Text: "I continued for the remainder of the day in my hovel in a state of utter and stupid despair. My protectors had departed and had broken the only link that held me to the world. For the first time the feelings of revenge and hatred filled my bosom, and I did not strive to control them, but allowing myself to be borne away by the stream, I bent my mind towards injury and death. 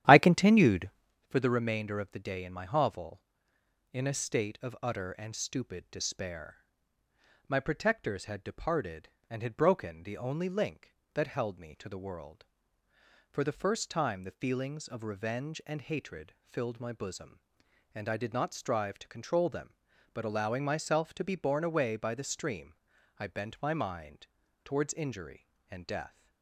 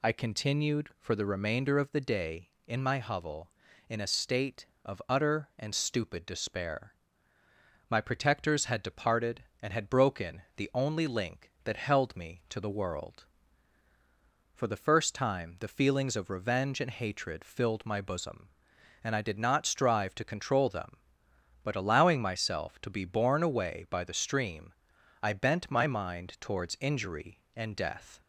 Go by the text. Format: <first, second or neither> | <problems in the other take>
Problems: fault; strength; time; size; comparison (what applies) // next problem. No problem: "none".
second | starts louder than the rest; strong; until 1.2 s; 11.5 dB // pauses between "mind" and "towards"; slight; at 24.2 s; 0.36 s long